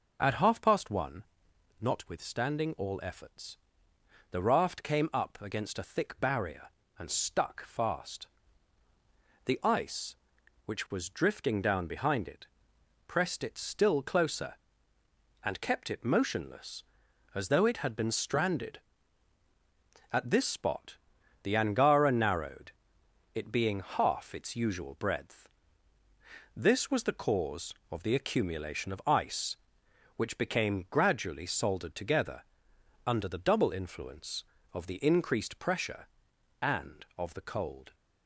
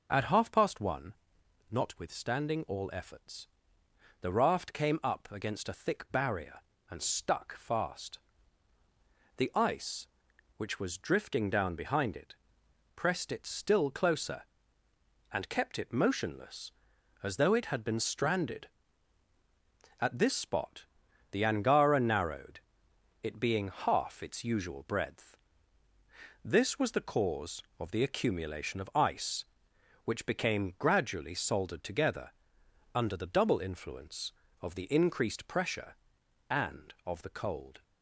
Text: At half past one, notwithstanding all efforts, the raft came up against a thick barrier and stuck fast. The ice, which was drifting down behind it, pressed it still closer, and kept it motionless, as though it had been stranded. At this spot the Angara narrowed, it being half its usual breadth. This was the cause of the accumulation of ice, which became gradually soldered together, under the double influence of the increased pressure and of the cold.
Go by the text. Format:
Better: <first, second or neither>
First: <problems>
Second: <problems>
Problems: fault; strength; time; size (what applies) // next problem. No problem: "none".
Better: neither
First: pauses between "spot" and "the"; noticeable; at 20.9 s; 0.46 s long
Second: pauses between "spot" and "the"; noticeable; at 20.8 s; 0.46 s long